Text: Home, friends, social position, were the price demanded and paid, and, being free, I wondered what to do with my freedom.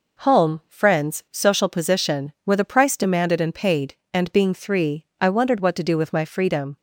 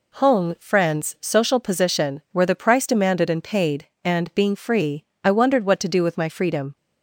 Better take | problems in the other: second | says "three" for "free"; at 4.5 s

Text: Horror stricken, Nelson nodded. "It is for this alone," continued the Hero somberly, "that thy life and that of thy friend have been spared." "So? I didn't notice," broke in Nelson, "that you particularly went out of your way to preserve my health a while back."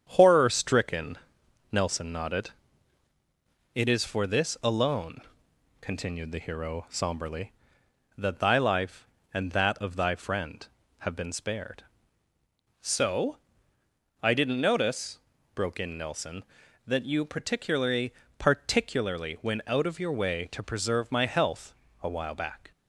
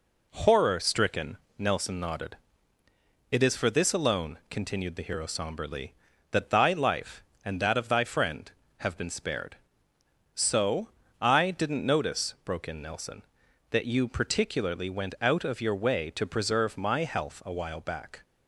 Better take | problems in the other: second | starts louder than the rest; strong; until 1.0 s; 8.5 dB // says "particularly" twice; at 18.3 s // pauses between "health" and "a"; slight; at 21.7 s; 0.28 s long

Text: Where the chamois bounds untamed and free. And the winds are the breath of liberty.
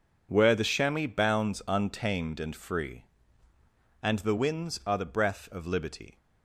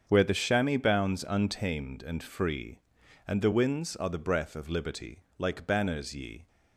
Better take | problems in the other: first | starts louder than the rest; strong; until 1.0 s; 7.5 dB // goes on to say "Like banners ye"; noticeable; from 5.3 s on; 1.1 s long

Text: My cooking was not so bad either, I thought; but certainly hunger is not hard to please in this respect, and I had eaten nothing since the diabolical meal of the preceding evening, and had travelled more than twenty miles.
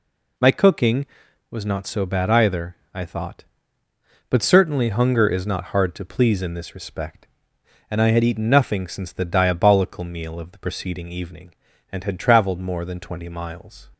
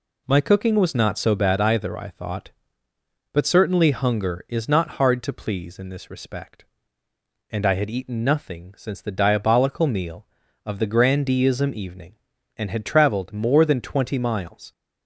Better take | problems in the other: first | says "grandeeism" for "preceding"; at 10.8 s

